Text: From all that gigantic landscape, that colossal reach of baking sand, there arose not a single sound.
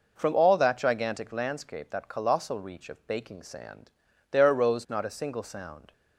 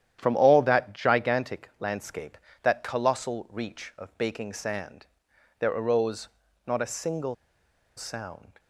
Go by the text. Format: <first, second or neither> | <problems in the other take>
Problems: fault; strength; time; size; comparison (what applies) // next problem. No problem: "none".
first | starts louder than the rest; strong; until 1.2 s; 10.5 dB // pauses between "arose" and "not"; at 6.2 s; 0.38 s long // pauses between "single" and "sound"; noticeable; at 7.3 s; 0.62 s long